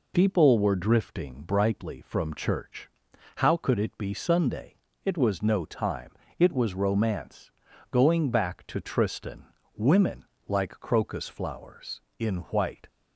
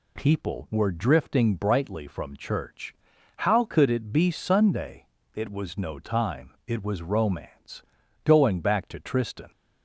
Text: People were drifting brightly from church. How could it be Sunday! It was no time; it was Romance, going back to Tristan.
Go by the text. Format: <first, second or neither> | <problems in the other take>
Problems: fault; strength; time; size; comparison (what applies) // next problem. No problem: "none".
second | goes on to say "Women like crocus flowers in white"; strong; from 9.7 s on; 3.1 s long